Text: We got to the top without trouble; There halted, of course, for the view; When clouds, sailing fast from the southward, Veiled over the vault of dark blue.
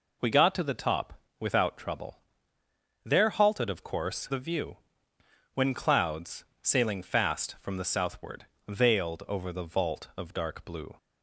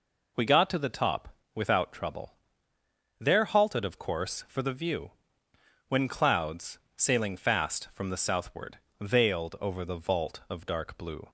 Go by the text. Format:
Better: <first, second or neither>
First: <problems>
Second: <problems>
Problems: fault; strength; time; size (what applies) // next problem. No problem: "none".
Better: second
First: pauses between "top" and "without"; slight; at 1.1 s; 0.20 s long // skips "for"; at 4.2 s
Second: pauses between "top" and "without"; slight; at 1.3 s; 0.20 s long